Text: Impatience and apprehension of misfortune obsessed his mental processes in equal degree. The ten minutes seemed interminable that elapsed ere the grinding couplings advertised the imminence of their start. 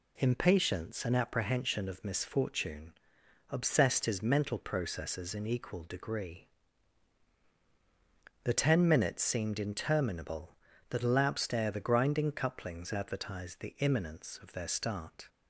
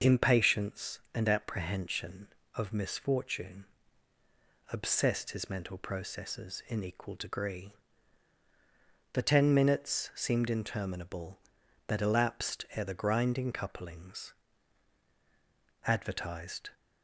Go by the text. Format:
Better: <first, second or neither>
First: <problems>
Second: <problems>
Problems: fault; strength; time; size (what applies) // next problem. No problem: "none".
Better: first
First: pauses between "misfortune" and "obsessed"; noticeable; at 2.9 s; 0.58 s long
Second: pauses between "misfortune" and "obsessed"; at 3.6 s; 1.0 s long // pauses between "couplings" and "advertised"; strong; at 14.3 s; 1.5 s long // stops before "the imminence of their start"; at 16.7 s